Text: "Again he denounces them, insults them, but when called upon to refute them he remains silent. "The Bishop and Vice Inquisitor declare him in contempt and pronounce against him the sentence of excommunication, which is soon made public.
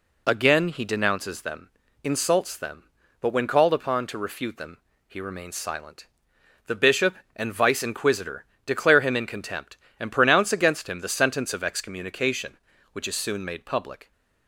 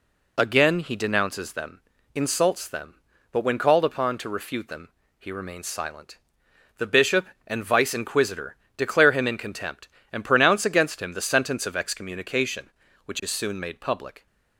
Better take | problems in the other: neither | pauses between "them" and "he"; slight; the same in both // pauses between "Inquisitor" and "declare"; slight; the same in both

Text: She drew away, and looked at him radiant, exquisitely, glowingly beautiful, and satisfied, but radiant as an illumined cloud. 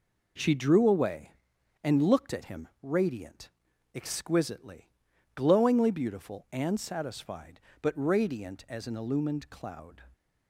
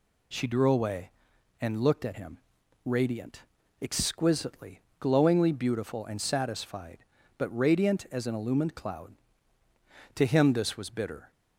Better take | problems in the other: first | pauses between "him" and "radiant"; noticeable; at 2.3 s; 0.48 s long // goes on to say "To him this was bitter"; noticeable; from 10.1 s on; 1.1 s long

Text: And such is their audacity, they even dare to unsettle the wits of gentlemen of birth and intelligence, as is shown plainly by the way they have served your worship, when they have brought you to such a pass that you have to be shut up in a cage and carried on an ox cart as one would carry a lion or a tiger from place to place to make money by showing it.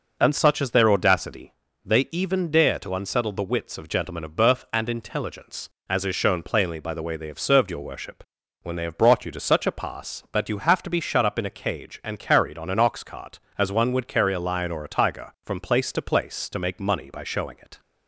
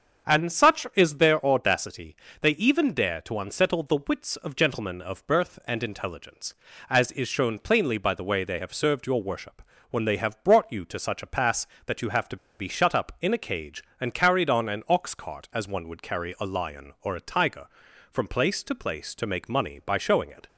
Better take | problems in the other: first | starts louder than the rest; strong; until 1.3 s; 7.5 dB // pauses between "to" and "be"; slight; at 12.3 s; 0.22 s long

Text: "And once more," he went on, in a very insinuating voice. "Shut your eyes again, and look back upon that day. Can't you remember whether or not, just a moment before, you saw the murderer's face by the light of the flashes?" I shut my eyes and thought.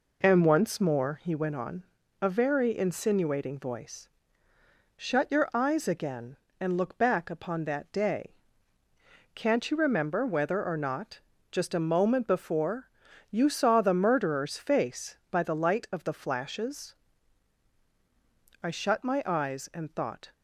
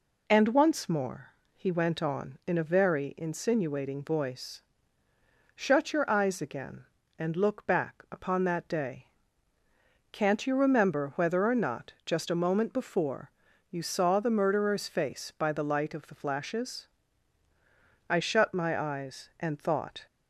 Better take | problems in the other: second | skips "in"; at 2.0 s

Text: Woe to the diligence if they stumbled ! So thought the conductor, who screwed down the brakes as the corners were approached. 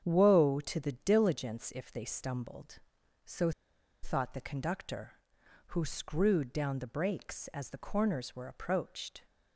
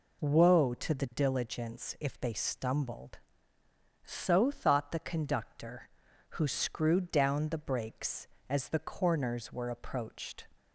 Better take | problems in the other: second | starts louder than the rest; strong; until 1.0 s; 8 dB // pauses between "So" and "thought"; noticeable; at 3.5 s; 0.51 s long

